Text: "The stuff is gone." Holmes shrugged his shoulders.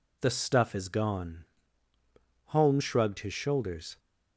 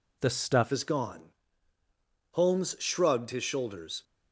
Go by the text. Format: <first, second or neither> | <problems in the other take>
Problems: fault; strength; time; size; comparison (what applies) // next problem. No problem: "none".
first | changes voice at "is"; from 0.7 s on; 3.3 s long